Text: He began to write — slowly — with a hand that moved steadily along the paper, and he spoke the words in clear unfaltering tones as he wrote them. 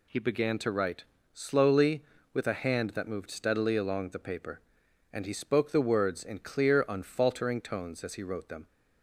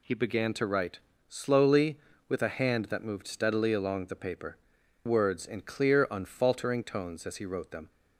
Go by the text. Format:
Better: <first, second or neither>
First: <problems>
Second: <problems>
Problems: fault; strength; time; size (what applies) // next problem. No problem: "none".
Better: first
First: none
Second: skips "and he spoke the"; at 4.8 s